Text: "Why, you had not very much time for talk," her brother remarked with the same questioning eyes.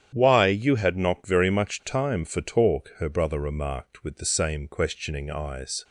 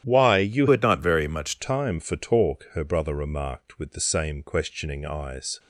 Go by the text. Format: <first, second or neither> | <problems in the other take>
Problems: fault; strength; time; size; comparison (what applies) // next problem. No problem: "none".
first | starts louder than the rest; strong; until 1.1 s; 10.5 dB; strong in the first // changes voice from "had" to "much"; from 0.7 to 1.5 s; 0.8 s long